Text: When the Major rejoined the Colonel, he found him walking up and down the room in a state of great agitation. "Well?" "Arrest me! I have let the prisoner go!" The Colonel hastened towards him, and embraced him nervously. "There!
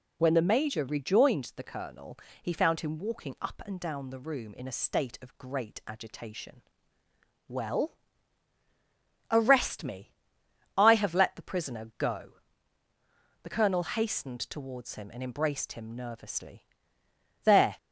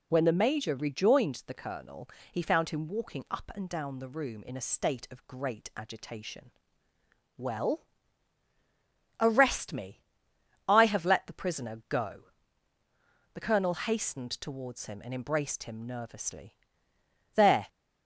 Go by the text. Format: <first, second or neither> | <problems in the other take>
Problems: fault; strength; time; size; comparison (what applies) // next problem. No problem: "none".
neither | none